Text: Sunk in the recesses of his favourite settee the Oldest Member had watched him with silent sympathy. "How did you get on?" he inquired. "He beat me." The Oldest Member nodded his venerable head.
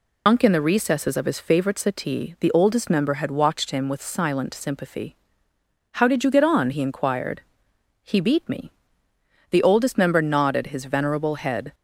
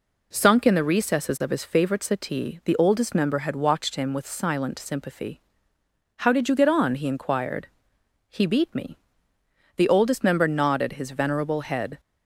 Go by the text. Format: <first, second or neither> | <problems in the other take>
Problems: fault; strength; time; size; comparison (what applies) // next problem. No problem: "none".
second | loses the start of "Sunk"; at 0.2 s; 160 ms